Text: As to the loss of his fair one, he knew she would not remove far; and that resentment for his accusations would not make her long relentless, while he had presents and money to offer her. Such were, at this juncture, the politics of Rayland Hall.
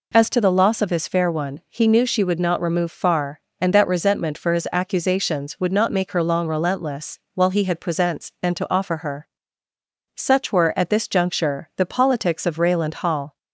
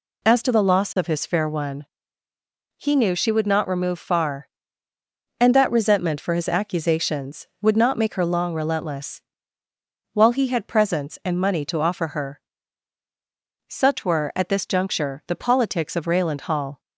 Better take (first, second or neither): second